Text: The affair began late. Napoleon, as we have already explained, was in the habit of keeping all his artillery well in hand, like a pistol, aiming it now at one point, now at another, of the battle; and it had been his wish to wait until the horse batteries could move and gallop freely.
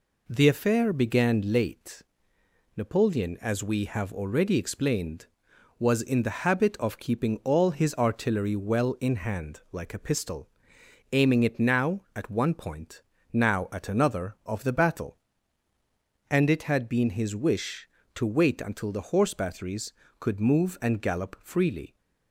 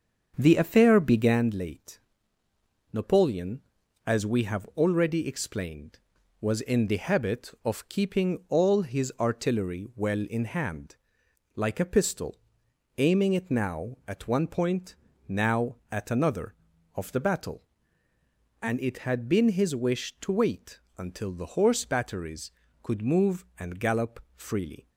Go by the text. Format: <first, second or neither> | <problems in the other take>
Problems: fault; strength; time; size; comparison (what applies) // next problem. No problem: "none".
first | starts louder than the rest; until 1.4 s; 7 dB // pauses between "wait" and "until"; slight; at 20.8 s; 0.16 s long // pauses between "gallop" and "freely"; slight; at 24.1 s; 0.16 s long